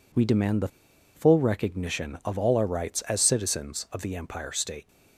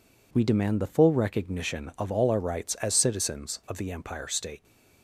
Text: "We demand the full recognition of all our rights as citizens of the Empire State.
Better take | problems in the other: second | pauses between "the" and "full"; noticeable; at 0.6 s; 0.47 s long

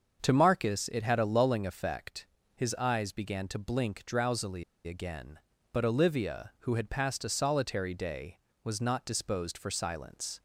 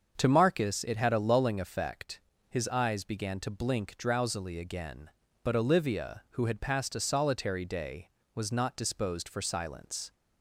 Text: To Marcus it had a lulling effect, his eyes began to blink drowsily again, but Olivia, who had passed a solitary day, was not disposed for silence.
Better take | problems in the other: second | starts louder than the rest; until 1.2 s; 7 dB; also in the second // pauses between "drowsily" and "again"; slight; at 4.6 s; 0.24 s long

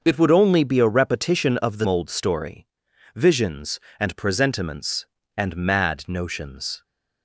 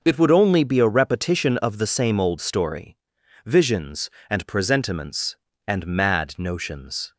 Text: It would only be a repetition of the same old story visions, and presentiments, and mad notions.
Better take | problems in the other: second | starts louder than the rest; until 1.0 s; 6.5 dB // skips "same"; at 1.8 s // pauses between "story" and "visions"; noticeable; at 2.6 s; 0.50 s long; noticeable in the second

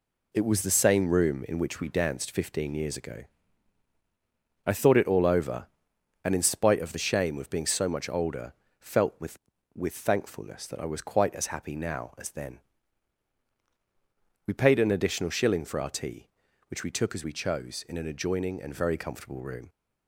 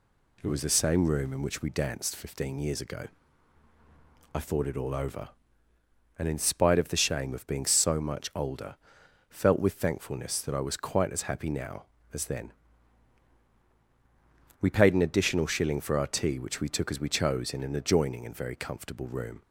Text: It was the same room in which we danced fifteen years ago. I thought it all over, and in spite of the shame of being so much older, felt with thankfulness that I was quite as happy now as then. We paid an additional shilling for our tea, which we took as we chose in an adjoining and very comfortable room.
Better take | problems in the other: second | says "with" twice; at 9.7 s

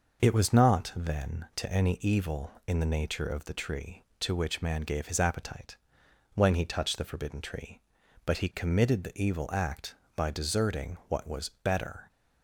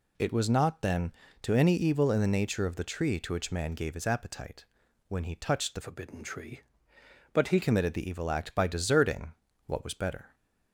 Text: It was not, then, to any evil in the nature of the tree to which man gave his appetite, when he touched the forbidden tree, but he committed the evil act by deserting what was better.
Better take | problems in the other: first | changes voice from "forbidden" to "he"; from 5.8 to 7.6 s; 1.8 s long // pauses between "deserting" and "what"; slight; at 9.3 s; 0.34 s long

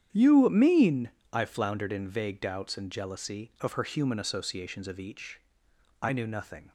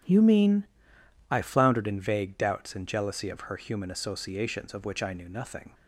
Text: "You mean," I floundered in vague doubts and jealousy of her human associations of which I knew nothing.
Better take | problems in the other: second | starts louder than the rest; strong; until 1.1 s; 9.5 dB; strong in the second // says "each" for "which"; at 4.9 s

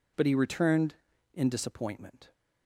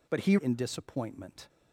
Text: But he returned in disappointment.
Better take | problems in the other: first | skips "returned"; at 0.3 s

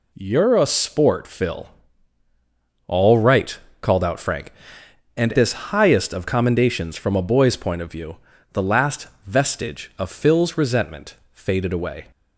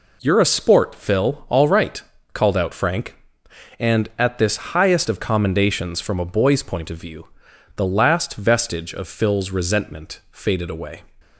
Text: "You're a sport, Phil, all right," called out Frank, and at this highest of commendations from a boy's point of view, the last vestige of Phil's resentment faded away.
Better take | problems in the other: second | skips "at"; at 5.3 s // pauses between "last" and "vestige"; slight; at 9.0 s; 0.18 s long // pauses between "resentment" and "faded"; slight; at 11.1 s; 0.16 s long

